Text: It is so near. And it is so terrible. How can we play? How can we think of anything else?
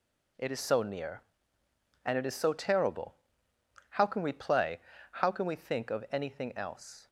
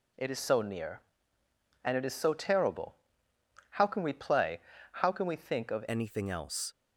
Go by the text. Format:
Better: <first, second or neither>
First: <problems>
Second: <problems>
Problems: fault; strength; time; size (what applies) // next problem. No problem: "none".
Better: first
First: none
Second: changes voice at "anything"; from 5.8 s on; 0.9 s long